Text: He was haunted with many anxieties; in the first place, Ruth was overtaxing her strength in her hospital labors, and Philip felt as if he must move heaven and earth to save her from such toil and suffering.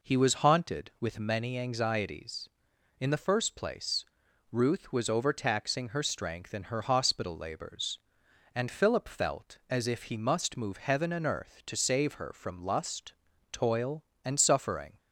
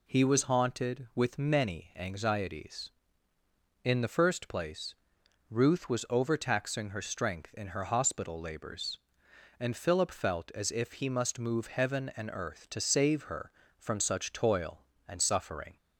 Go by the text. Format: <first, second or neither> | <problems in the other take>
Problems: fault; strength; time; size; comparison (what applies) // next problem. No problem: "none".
second | says "lust" for "such"; at 12.6 s